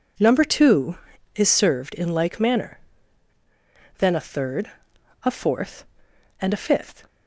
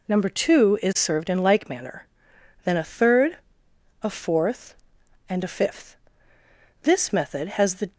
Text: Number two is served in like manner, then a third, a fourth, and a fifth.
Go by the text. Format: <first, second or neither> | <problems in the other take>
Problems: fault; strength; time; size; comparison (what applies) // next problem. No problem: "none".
first | goes on to say "This method has the"; noticeable; from 6.8 s on; 1.1 s long